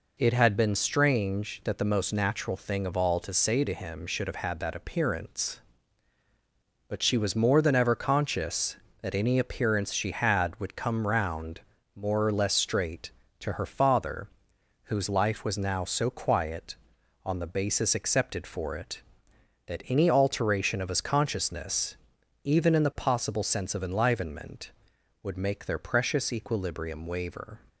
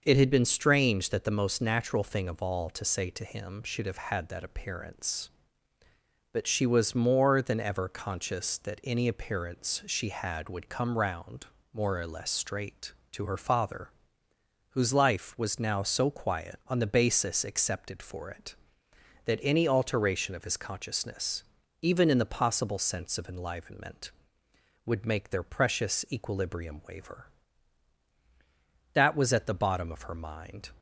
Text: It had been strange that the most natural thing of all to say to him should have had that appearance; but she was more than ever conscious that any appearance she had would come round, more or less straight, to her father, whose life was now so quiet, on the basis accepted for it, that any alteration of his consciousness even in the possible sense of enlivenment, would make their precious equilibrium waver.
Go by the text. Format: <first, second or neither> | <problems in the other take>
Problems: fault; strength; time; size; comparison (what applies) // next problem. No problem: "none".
first | starts louder than the rest; until 1.0 s; 6 dB // pauses between "consciousness" and "even"; at 21.4 s; 0.40 s long; noticeable in the first // goes on to say "THAT was at the bottom of her mind"; strong; from 28.9 s on; 1.7 s long